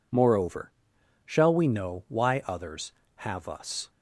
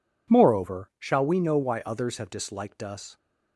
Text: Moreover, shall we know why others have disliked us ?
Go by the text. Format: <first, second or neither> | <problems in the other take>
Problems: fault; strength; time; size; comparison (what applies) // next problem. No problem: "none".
second | skips "disliked"; at 3.4 s